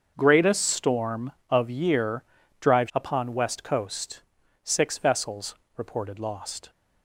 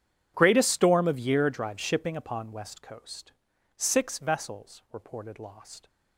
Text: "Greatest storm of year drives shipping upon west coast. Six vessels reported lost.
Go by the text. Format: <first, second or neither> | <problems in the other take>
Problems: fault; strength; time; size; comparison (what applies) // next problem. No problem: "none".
second | starts louder than the rest; until 1.1 s; 6.5 dB // pauses between "year" and "drives"; at 2.2 s; 0.38 s long // skips "shipping"; at 2.9 s // pauses between "vessels" and "reported"; slight; at 5.5 s; 0.20 s long